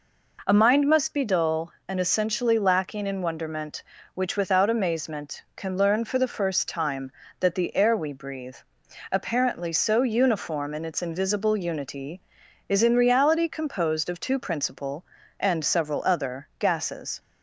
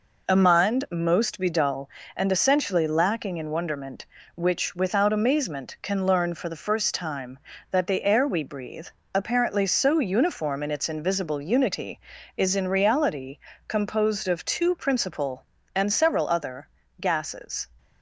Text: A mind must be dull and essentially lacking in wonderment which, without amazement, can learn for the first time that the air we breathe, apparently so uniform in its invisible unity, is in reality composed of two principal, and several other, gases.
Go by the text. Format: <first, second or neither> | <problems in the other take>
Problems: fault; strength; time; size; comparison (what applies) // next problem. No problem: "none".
first | says "most" for "must"; at 0.9 s // pauses between "reality" and "composed"; slight; at 13.3 s; 0.30 s long